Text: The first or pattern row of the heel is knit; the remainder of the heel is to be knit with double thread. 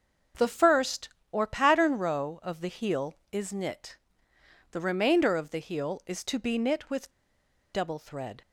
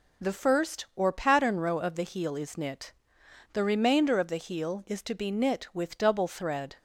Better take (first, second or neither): second